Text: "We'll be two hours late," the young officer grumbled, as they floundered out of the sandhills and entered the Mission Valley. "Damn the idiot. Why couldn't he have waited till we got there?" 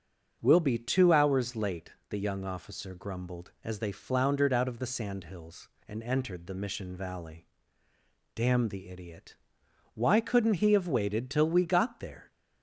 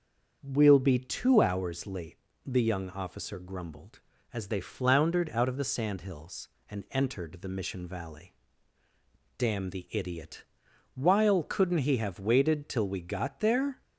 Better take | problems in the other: first | starts louder than the rest; until 1.4 s; 7 dB; also in the first // says "While" for "Why"; at 10.9 s

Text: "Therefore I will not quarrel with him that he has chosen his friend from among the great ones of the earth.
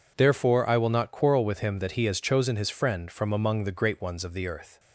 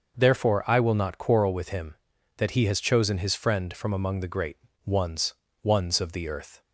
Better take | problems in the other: first | starts louder than the rest; noticeable; until 1.2 s; 6 dB // pauses between "great" and "ones"; slight; at 4.5 s; 0.28 s long // says "ones" twice; at 5.6 s

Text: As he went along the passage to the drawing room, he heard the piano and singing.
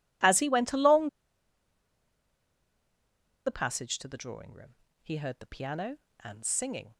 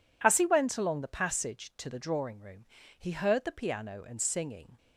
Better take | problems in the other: second | pauses between "along" and "the"; strong; at 1.0 s; 2.3 s long

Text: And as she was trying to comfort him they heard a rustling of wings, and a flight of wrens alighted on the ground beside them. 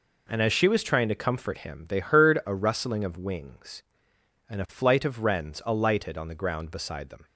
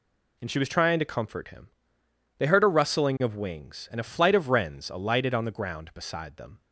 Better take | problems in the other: first | skips "as"; at 0.4 s // pauses between "him" and "they"; noticeable; at 1.6 s; 0.68 s long

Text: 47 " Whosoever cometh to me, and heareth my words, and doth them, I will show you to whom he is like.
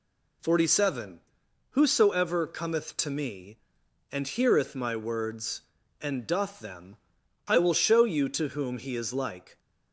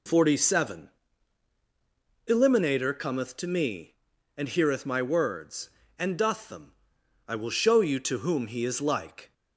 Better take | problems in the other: first | says "Eliminator" for "Whosoever"; at 2.2 s

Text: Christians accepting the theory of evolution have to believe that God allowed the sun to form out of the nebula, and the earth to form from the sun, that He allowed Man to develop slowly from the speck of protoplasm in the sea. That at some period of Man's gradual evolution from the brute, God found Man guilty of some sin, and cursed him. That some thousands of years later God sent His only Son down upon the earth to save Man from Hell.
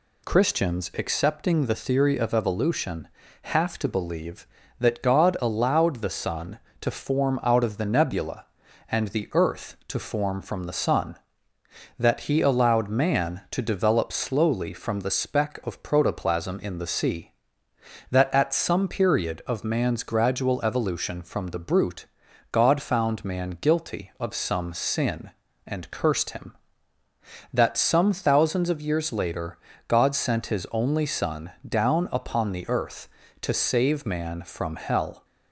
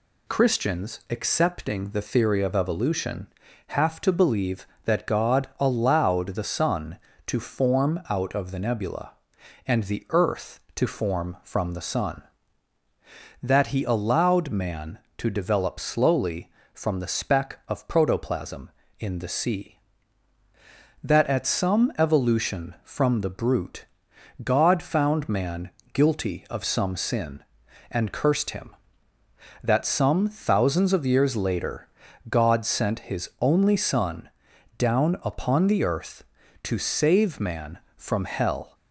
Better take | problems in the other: first | skips "period of Man's gradual"; at 21.9 s // pauses between "Man" and "guilty"; slight; at 25.6 s; 0.24 s long // pauses between "later" and "God"; at 31.8 s; 0.42 s long; slight in the first // pauses between "Son" and "down"; noticeable; at 34.2 s; 0.48 s long; slight in the first

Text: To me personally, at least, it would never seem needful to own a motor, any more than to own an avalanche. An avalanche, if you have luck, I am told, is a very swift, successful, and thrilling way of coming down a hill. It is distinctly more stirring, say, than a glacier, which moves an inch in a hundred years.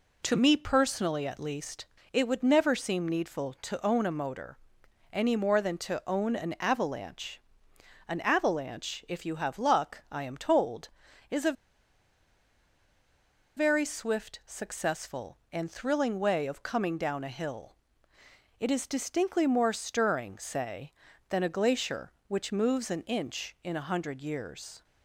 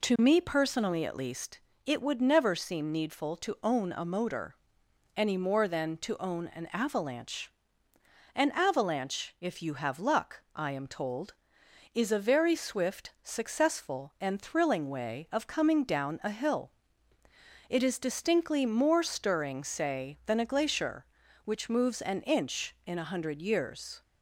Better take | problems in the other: second | pauses between "a" and "very"; strong; at 11.5 s; 2.0 s long

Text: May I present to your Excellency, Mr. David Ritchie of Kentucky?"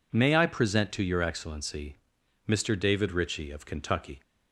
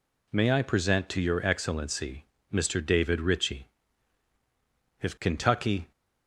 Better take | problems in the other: first | says "if" for "of"; at 4.9 s

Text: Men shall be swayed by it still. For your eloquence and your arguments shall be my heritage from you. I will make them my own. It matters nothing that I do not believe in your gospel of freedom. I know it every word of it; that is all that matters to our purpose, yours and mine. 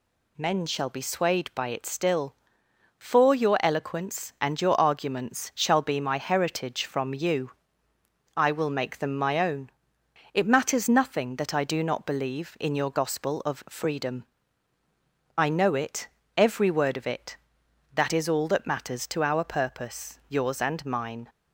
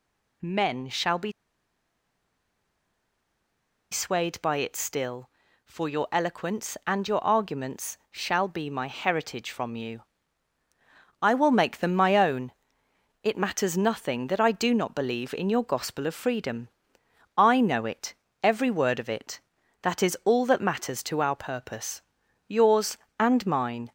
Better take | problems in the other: first | pauses between "be" and "swayed"; strong; at 1.3 s; 2.5 s long // pauses between "it" and "every"; slight; at 18.1 s; 0.28 s long; slight in the first

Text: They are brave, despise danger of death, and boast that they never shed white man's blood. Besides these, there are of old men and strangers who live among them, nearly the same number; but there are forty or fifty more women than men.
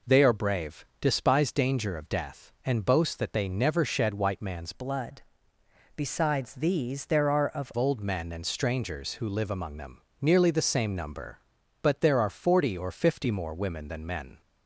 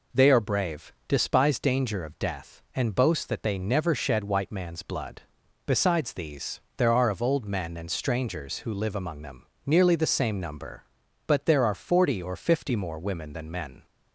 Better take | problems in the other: second | changes voice from "blood" to "of"; from 4.7 to 7.7 s; 3.0 s long

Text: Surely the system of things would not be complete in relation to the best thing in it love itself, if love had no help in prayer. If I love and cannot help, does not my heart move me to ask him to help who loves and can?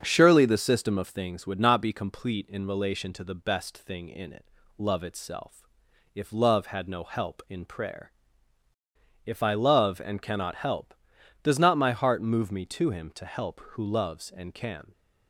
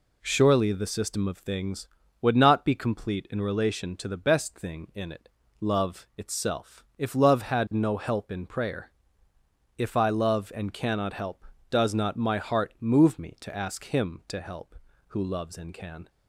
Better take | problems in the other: second | starts louder than the rest; until 1.0 s; 7 dB // pauses between "it" and "love"; slight; at 4.4 s; 0.32 s long; slight in the second // skips "ask"; at 12.9 s

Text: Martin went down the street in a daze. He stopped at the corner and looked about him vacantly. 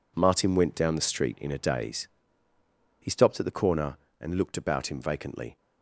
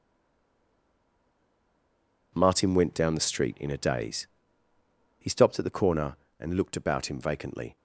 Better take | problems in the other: first | stays silent before the first word; until 2.3 s; 2.3 s long

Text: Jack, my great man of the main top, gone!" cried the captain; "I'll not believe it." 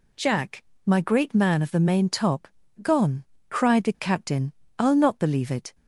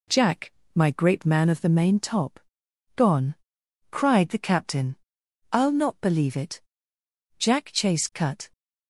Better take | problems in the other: first | goes on to say "Jack Chase cut"; noticeable; from 7.3 s on; 1.1 s long

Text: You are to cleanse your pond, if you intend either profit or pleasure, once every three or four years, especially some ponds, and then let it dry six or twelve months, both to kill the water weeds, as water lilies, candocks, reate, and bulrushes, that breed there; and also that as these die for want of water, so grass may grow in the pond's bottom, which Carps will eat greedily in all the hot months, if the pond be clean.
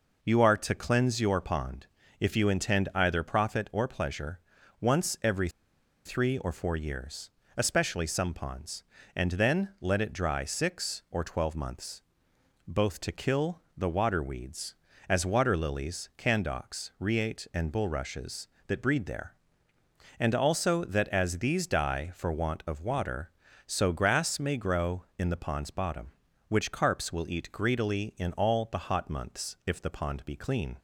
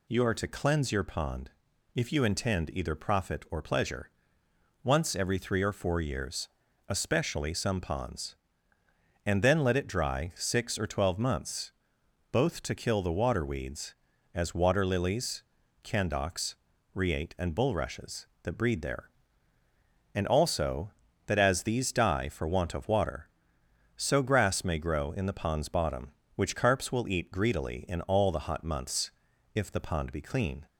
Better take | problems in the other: second | pauses between "every" and "three"; noticeable; at 5.4 s; 0.56 s long // pauses between "kill" and "the"; slight; at 13.6 s; 0.16 s long

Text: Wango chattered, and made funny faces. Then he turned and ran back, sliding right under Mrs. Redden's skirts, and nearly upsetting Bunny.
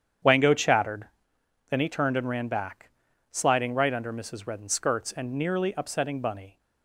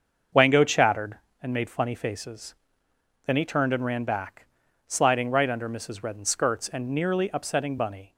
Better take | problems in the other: second | starts louder than the rest; strong; until 1.8 s; 8.5 dB; also in the second // skips "and made funny faces"; at 1.3 s

